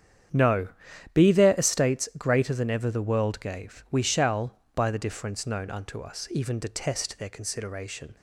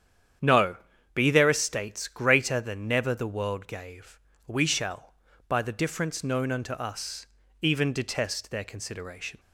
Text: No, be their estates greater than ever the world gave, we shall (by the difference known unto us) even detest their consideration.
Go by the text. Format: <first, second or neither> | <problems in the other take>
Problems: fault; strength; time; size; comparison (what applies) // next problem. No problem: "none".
first | starts louder than the rest; strong; until 1.8 s; 9 dB; strong in the first // says "never" for "ever"; at 2.8 s